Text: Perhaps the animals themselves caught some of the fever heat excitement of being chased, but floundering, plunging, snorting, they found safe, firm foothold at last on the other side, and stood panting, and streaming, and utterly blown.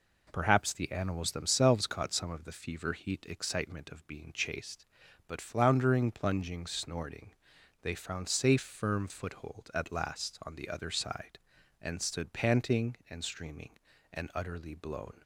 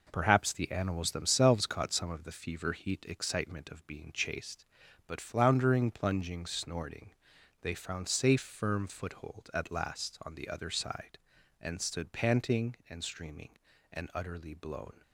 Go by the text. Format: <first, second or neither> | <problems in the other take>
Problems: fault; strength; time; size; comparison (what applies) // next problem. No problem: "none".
first | gets quieter; throughout; 7 dB